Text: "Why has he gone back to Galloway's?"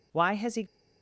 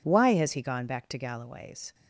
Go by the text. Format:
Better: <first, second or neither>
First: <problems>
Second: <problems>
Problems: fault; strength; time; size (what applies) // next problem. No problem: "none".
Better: second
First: stops before "gone back to Galloway's"; at 0.6 s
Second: none